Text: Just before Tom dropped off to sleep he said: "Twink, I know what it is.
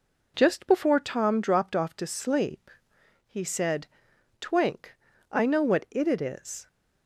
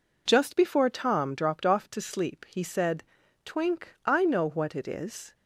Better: second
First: pauses between "sleep" and "he"; noticeable; at 2.6 s; 0.56 s long // says "it" twice; at 6.0 s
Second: none

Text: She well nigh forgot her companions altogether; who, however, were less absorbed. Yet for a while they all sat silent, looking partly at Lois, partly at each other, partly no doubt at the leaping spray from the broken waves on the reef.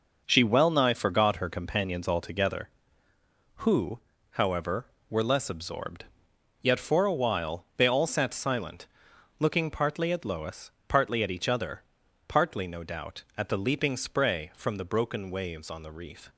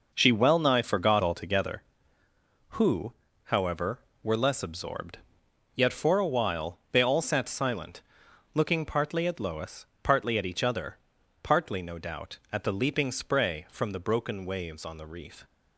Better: first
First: none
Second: skips "her companions"; at 1.2 s

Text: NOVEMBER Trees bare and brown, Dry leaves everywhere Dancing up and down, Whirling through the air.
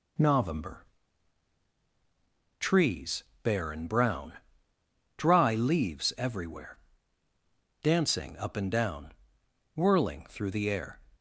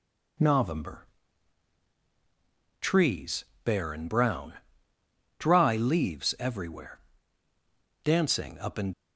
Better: first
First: pauses between "NOVEMBER" and "Trees"; strong; at 0.8 s; 1.7 s long // pauses between "Trees" and "bare"; slight; at 3.2 s; 0.20 s long // pauses between "everywhere" and "Dancing"; at 6.7 s; 1.0 s long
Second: pauses between "NOVEMBER" and "Trees"; strong; at 1.0 s; 1.7 s long // pauses between "Trees" and "bare"; slight; at 3.4 s; 0.20 s long // pauses between "everywhere" and "Dancing"; at 6.9 s; 1.0 s long // stops before "down Whirling through the air"; at 8.9 s

